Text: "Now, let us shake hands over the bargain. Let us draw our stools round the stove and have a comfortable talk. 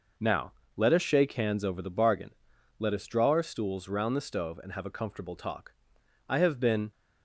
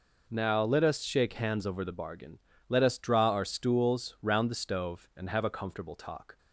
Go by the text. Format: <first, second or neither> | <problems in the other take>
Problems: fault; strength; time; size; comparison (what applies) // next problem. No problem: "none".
second | goes on to say "I have been"; noticeable; from 6.2 s on; 0.62 s long